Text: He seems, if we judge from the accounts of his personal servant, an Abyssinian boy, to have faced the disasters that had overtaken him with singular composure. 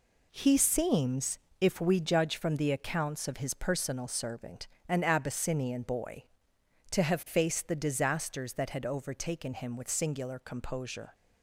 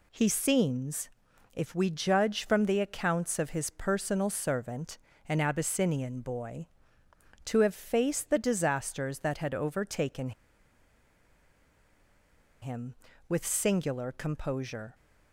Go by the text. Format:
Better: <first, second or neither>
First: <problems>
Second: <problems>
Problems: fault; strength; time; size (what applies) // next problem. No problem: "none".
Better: first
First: none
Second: pauses between "overtaken" and "him"; strong; at 10.3 s; 2.3 s long